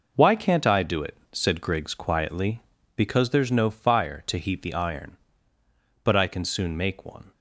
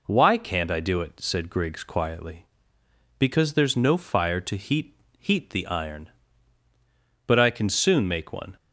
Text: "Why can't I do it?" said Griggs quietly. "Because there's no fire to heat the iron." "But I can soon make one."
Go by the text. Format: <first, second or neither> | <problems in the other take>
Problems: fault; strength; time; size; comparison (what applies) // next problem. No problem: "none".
first | says "heat" twice; at 5.1 s